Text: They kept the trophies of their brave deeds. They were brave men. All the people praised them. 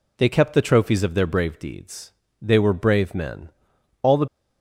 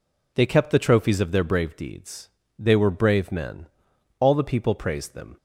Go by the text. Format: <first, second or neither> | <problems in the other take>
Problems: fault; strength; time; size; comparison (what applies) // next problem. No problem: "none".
second | stops before "people praised them"; at 4.2 s